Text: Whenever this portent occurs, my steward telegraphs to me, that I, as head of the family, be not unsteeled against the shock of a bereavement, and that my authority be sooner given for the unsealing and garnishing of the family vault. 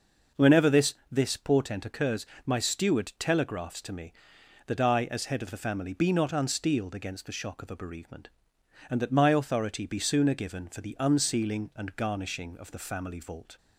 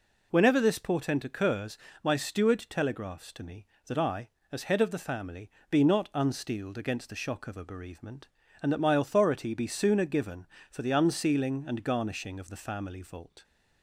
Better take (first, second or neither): second